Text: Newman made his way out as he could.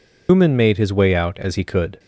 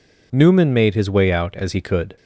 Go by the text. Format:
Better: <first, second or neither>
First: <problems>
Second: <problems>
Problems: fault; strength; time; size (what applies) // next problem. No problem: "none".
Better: second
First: loses the start of "Newman"; at 0.2 s; 145 ms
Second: none